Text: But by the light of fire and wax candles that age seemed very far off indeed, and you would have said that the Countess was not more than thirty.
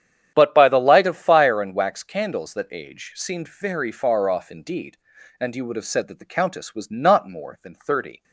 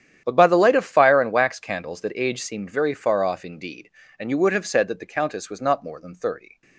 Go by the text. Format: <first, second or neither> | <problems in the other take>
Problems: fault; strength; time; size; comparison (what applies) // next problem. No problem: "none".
neither | starts louder than the rest; strong; the same in both